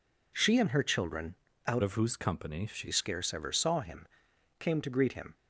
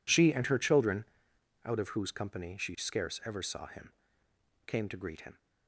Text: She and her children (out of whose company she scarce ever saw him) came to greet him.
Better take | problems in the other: second | changes voice from "of" to "she"; from 1.8 to 2.8 s; 1.0 s long

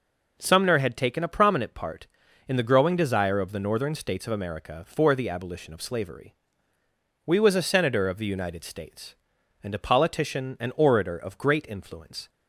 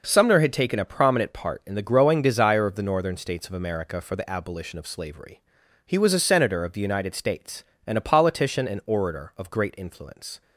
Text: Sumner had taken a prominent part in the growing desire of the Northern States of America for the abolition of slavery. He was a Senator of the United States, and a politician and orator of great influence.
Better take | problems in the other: second | says "We" for "He"; at 7.2 s

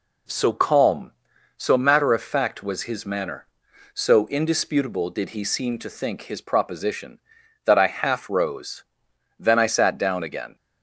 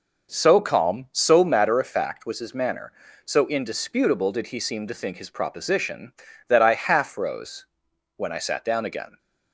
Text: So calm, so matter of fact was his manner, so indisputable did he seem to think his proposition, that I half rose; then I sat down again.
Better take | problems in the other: first | says "when" for "then"; at 8.1 s

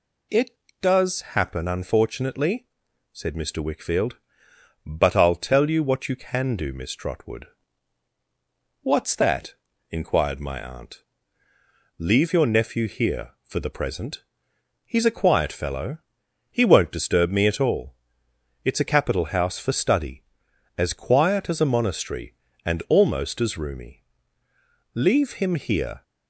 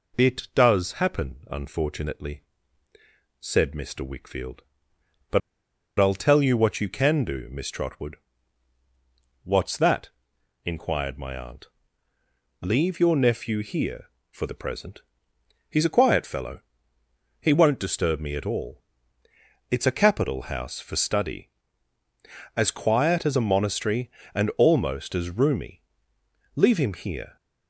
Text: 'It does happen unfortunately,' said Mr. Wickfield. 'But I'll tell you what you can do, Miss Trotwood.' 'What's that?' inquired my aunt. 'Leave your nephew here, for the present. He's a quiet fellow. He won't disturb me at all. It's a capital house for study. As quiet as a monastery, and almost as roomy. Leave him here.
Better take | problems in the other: first | pauses between "But" and "I'll"; noticeable; at 5.4 s; 0.59 s long

